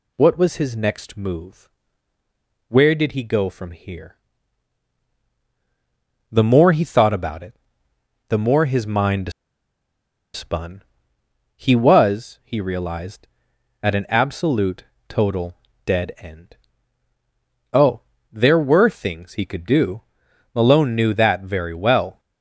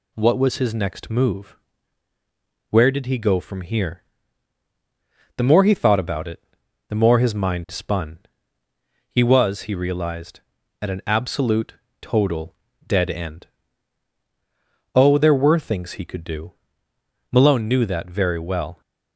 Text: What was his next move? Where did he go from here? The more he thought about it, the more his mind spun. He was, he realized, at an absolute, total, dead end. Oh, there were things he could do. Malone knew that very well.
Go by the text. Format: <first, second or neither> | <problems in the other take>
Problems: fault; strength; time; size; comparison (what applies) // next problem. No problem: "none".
second | pauses between "mind" and "spun"; at 9.3 s; 1.0 s long